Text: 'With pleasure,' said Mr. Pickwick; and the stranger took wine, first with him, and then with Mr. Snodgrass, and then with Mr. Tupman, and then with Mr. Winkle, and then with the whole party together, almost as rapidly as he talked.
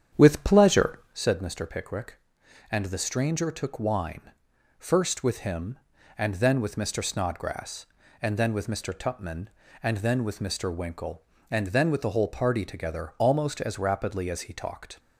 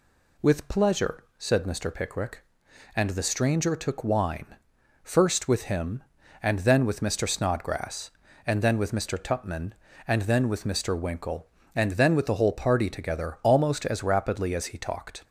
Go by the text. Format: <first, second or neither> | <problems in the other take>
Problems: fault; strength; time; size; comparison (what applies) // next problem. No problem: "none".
second | starts louder than the rest; strong; until 1.4 s; 8.5 dB